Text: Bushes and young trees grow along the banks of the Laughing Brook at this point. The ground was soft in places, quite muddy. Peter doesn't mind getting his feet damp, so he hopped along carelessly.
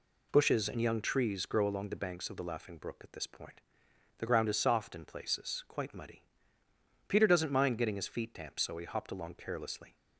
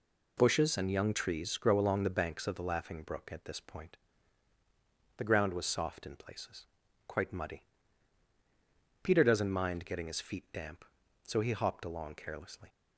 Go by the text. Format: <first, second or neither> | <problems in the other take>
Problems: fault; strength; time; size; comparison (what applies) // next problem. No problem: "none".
second | says "is" for "was"; at 4.4 s